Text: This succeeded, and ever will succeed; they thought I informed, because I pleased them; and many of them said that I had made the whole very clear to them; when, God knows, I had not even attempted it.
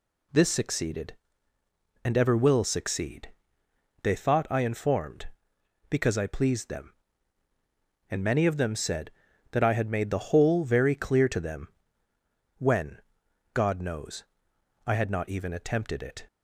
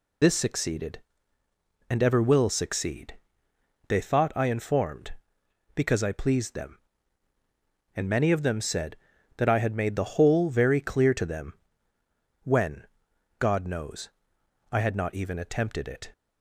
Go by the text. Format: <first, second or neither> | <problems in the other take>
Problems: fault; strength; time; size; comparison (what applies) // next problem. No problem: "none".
first | loses the start of "This"; at 0.2 s; 55 ms